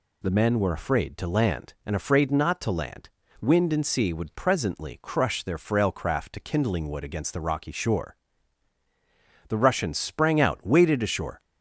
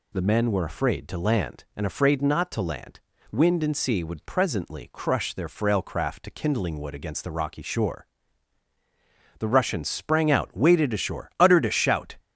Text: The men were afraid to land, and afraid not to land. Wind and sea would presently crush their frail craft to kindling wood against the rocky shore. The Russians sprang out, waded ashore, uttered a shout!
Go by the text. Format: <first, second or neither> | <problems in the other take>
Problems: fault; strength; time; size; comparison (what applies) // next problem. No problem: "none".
second | stops before "uttered a shout"; at 11.3 s